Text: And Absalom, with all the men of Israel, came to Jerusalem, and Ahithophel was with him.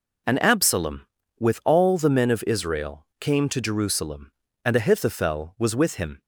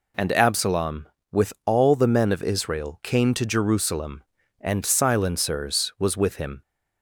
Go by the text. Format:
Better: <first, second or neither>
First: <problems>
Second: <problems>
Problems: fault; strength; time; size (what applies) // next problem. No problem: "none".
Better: first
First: none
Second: says "Silencers" for "Ahithophel"; at 4.8 s